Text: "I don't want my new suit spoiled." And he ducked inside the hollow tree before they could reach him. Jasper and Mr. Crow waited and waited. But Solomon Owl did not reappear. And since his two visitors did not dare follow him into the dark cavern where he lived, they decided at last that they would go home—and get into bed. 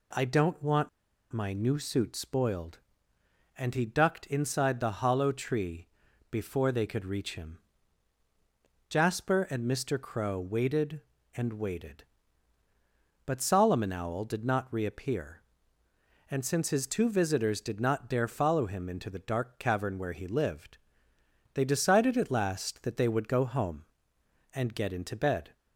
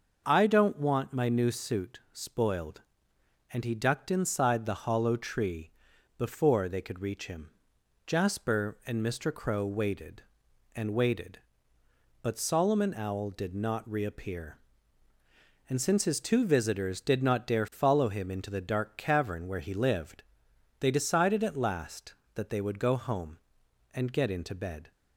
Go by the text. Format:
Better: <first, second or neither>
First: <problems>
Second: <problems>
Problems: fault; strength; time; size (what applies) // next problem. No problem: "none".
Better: second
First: pauses between "want" and "my"; at 0.8 s; 0.43 s long // pauses between "tree" and "before"; at 5.8 s; 0.42 s long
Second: pauses between "tree" and "before"; noticeable; at 5.6 s; 0.48 s long